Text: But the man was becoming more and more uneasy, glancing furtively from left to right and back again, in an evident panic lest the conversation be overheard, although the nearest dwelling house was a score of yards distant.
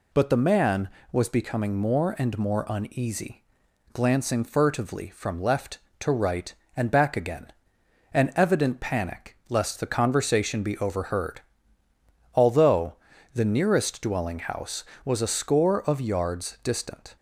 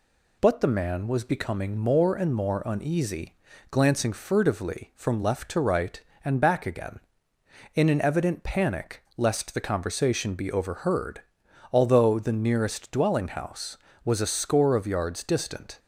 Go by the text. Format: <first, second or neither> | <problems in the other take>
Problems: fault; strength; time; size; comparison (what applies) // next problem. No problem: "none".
second | skips "in"; at 7.7 s // pauses between "although" and "the"; at 12.9 s; 0.38 s long